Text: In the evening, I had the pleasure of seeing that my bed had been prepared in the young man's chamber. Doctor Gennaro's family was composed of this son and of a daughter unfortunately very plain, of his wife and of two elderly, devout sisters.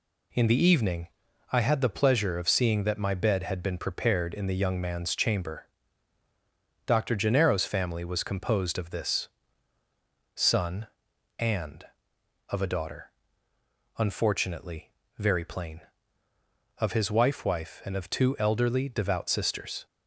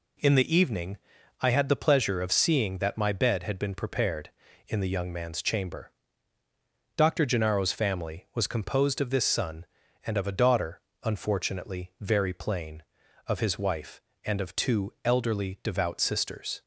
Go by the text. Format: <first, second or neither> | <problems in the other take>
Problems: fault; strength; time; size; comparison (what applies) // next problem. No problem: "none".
second | pauses between "this" and "son"; at 9.2 s; 1.0 s long // pauses between "daughter" and "unfortunately"; noticeable; at 13.0 s; 0.88 s long; slight in the second // pauses between "unfortunately" and "very"; slight; at 14.8 s; 0.30 s long // says "wife" twice; at 17.4 s